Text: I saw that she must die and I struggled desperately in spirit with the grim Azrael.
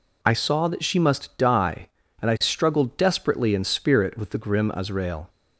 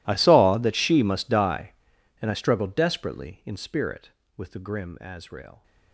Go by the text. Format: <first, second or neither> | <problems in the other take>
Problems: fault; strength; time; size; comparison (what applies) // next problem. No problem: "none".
first | gets quieter; strong; throughout; 25 dB